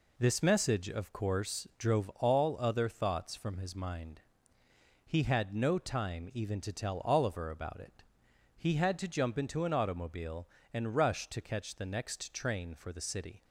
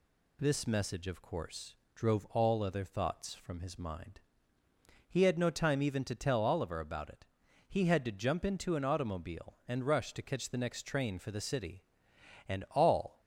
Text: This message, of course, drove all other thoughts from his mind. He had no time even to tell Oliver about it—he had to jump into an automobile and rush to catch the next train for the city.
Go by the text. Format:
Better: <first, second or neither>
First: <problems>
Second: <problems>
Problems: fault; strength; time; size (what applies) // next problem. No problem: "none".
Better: first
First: none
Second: goes on to say "And all"; noticeable; from 12.4 s on; 0.72 s long